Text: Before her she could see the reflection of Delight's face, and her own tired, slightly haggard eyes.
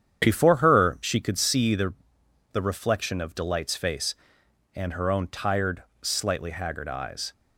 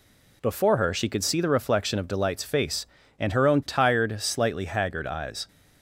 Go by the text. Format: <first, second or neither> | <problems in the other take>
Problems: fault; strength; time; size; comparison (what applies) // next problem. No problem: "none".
second | starts louder than the rest; strong; until 1.2 s; 8.5 dB // says "the" twice; at 2.5 s